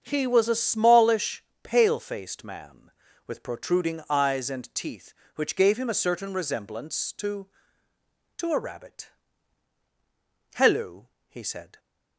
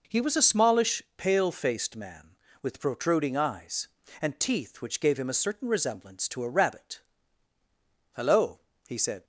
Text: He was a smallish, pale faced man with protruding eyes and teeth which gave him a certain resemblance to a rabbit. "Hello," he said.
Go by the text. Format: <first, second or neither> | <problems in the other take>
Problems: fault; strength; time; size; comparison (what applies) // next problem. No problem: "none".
second | starts louder than the rest; until 1.0 s; 7 dB // says "to" twice; at 8.3 s